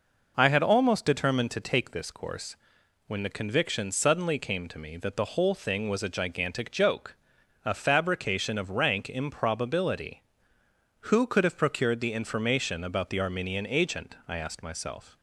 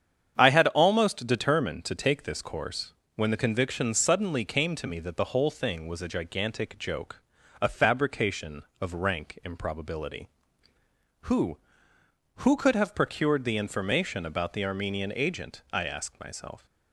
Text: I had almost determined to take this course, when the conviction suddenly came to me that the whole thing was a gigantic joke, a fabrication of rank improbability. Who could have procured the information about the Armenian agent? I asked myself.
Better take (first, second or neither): first